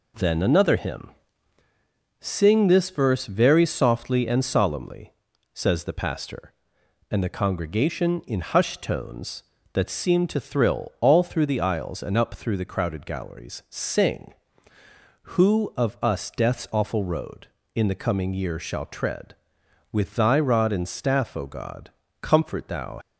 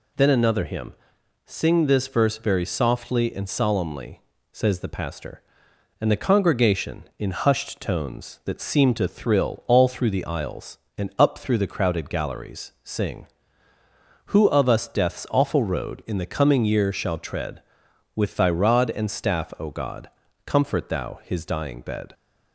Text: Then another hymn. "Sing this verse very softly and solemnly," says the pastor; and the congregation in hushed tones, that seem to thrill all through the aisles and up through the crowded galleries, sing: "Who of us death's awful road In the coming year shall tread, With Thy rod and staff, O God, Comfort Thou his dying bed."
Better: second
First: stops before "his dying bed"; at 23.0 s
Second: none

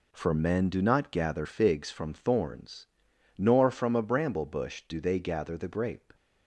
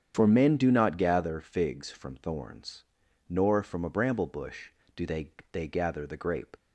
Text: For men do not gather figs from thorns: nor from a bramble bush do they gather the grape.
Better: first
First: none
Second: starts louder than the rest; strong; until 1.1 s; 8.5 dB // says "they" twice; at 5.5 s

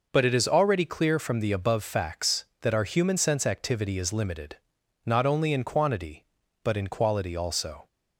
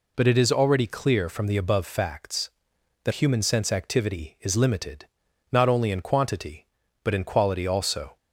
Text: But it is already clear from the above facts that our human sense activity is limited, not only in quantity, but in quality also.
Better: first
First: none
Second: skips "our"; at 3.1 s

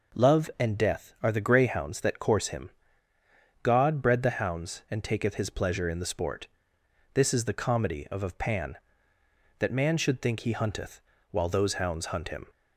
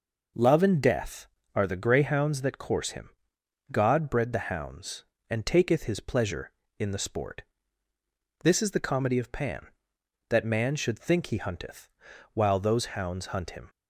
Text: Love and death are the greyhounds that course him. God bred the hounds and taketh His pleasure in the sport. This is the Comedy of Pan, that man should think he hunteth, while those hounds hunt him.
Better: second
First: says "of" twice; at 8.2 s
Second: none

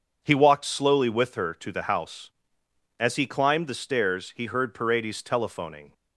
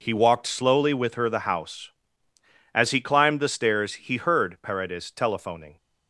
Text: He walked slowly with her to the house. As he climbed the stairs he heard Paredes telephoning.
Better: first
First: none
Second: skips "to"; at 1.2 s

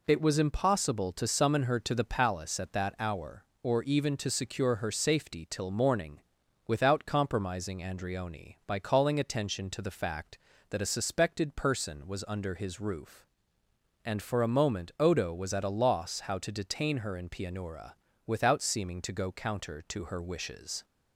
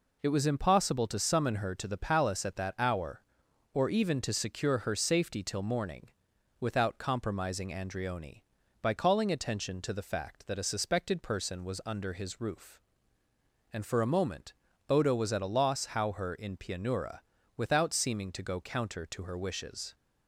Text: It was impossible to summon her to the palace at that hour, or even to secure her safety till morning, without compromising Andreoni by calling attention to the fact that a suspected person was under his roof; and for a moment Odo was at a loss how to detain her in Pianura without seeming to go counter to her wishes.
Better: first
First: pauses between "Pianura" and "without"; slight; at 17.9 s; 0.32 s long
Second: pauses between "moment" and "Odo"; at 14.5 s; 0.38 s long // skips "to detain"; at 16.1 s // pauses between "Pianura" and "without"; slight; at 17.2 s; 0.34 s long

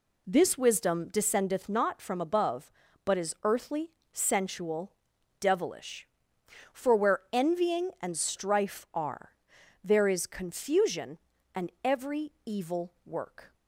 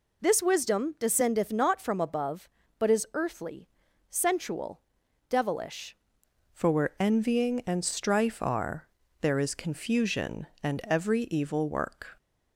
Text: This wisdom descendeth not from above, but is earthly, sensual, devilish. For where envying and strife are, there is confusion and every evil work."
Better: first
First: none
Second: changes voice at "For"; from 6.5 s on; 5.6 s long

